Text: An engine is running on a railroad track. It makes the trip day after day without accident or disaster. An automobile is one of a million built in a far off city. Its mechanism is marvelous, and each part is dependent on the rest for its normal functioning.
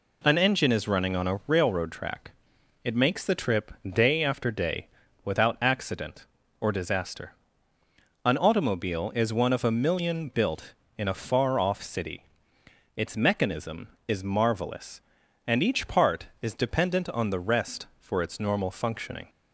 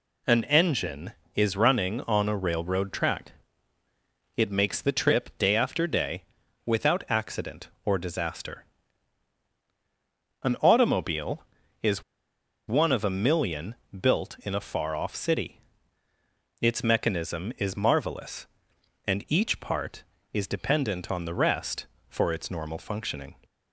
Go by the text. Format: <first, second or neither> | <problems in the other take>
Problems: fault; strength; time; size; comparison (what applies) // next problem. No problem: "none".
first | pauses between "day" and "without"; at 6.2 s; 0.42 s long; also in the first // pauses between "is" and "one"; noticeable; at 12.0 s; 0.66 s long // pauses between "million" and "built"; slight; at 13.7 s; 0.26 s long